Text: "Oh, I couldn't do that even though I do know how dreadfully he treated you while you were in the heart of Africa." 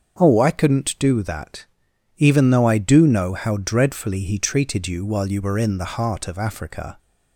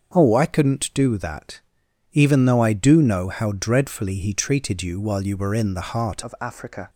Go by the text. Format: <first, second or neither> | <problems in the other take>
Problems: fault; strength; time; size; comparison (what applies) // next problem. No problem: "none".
first | starts louder than the rest; until 1.1 s; 7 dB; also in the first // pauses between "that" and "even"; noticeable; at 1.6 s; 0.54 s long; noticeable in the first // changes voice at "of"; from 6.2 s on; 0.6 s long